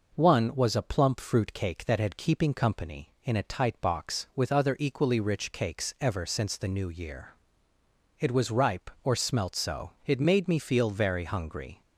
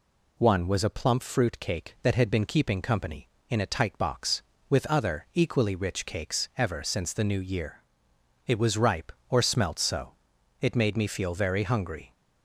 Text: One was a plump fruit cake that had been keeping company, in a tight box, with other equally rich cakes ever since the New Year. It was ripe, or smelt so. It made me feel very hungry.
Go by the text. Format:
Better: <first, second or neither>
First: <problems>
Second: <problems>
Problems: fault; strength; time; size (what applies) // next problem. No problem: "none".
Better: second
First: skips "been"; at 2.1 s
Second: none